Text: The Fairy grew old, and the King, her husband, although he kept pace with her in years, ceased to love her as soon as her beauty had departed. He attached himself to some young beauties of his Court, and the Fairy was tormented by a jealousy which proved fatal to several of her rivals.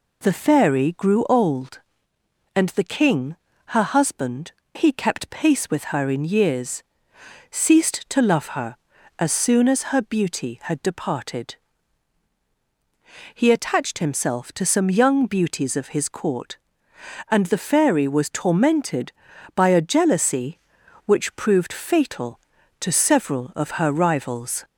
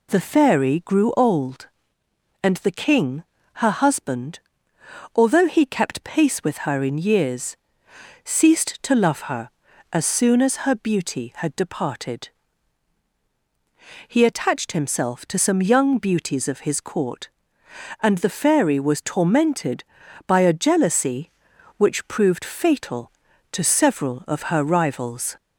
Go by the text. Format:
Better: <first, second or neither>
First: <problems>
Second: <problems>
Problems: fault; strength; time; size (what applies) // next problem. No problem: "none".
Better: second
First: skips "although"; at 4.6 s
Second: none